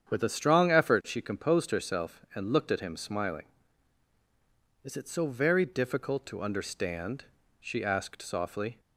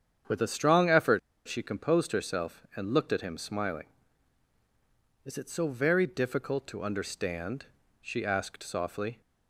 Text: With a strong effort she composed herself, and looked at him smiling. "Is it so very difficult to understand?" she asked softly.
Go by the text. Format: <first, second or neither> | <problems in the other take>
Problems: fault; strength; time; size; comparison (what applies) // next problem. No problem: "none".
first | starts louder than the rest; strong; until 1.5 s; 8 dB; strong in the first // pauses between "effort" and "she"; slight; at 1.1 s; 0.26 s long